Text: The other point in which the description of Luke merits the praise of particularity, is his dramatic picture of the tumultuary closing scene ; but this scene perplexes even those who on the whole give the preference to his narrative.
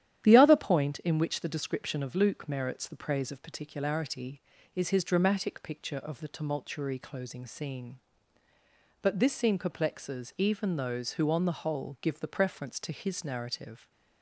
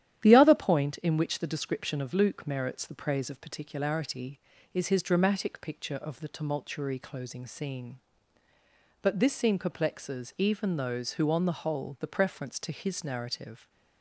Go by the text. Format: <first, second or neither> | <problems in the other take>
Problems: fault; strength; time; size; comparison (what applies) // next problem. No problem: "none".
first | starts louder than the rest; strong; until 1.2 s; 11 dB; strong in the first // skips "give"; at 11.9 s